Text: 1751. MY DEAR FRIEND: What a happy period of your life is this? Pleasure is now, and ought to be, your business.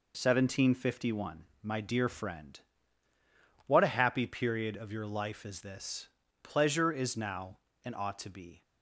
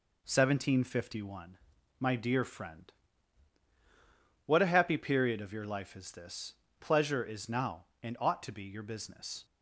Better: second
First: stops before "your business"; at 8.6 s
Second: none

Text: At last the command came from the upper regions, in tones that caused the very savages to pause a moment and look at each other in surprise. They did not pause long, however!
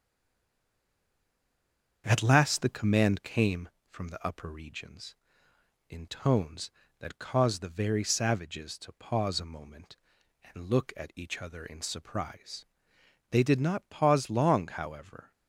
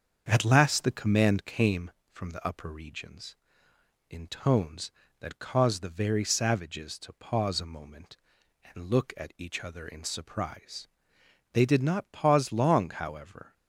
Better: second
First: stays silent before the first word; noticeable; until 2.0 s; 2.0 s long // starts louder than the rest; strong; until 3.0 s; 7 dB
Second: starts louder than the rest; strong; until 1.2 s; 7 dB

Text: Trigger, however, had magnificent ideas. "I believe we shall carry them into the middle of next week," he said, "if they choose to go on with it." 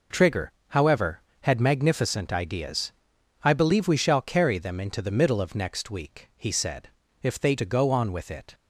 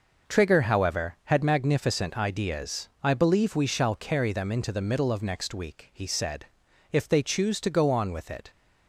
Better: second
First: skips "choose"; at 7.5 s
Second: none

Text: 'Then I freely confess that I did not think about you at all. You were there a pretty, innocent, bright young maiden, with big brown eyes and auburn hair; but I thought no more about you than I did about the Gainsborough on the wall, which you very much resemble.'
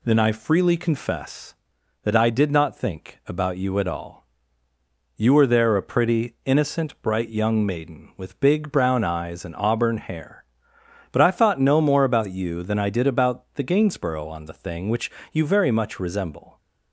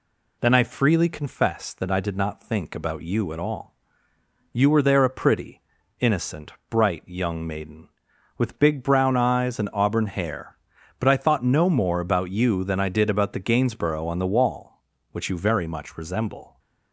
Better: second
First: says "thing" for "wall"; at 14.5 s // pauses between "which" and "you"; slight; at 15.1 s; 0.20 s long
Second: none

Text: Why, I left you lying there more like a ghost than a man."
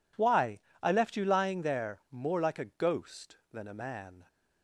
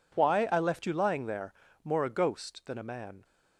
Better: first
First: none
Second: pauses between "there" and "more"; slight; at 1.5 s; 0.30 s long // skips "like"; at 2.0 s

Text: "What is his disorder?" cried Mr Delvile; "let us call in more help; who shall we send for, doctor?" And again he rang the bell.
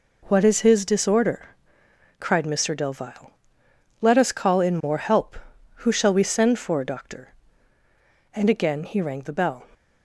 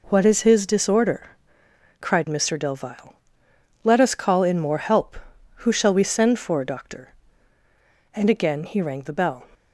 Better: neither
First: none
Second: none

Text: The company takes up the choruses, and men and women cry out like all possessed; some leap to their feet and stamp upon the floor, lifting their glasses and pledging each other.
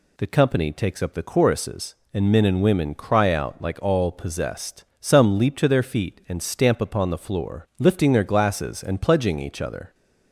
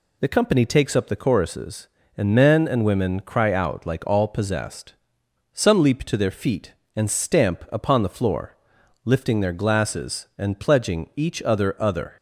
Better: first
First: none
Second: says "other" twice; at 11.8 s

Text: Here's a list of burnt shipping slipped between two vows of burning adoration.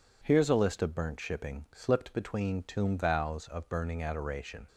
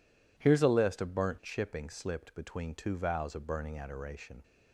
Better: second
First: says "tomb" for "two"; at 2.6 s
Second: none

